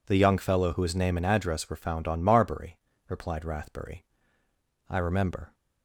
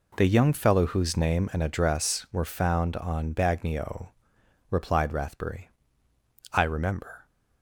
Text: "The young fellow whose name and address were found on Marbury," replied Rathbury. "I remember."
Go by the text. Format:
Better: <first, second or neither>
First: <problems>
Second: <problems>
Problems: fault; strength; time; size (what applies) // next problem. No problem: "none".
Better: first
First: none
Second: says "Bagnio" for "Marbury"; at 3.3 s